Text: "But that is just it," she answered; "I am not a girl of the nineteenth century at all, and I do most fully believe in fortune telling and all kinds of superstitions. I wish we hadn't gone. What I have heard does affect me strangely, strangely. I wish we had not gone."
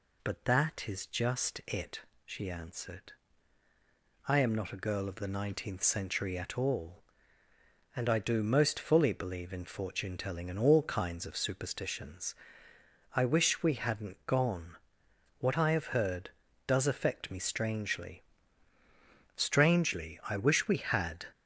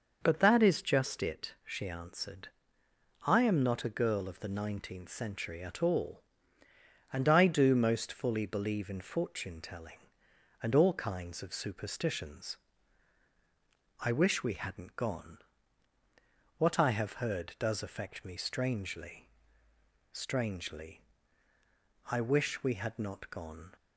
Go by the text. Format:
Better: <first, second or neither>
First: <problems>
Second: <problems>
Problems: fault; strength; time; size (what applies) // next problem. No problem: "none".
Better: second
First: stops before "not gone"; at 21.3 s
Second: none